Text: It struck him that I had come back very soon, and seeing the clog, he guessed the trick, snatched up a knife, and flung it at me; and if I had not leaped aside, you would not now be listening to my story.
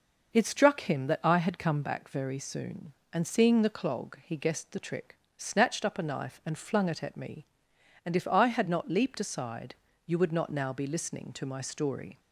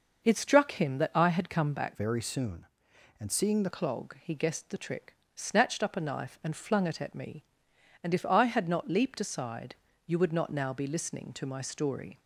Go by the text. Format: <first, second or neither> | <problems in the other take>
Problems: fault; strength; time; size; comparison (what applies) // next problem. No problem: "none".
first | changes voice from "very" to "the"; from 1.9 to 3.7 s; 1.8 s long